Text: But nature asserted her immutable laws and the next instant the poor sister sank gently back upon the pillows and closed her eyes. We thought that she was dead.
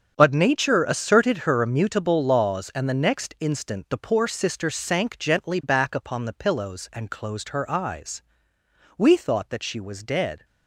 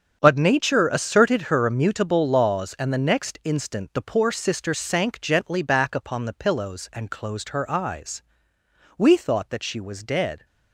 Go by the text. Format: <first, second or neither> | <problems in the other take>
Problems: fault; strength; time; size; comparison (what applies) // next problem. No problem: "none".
neither | starts louder than the rest; strong; the same in both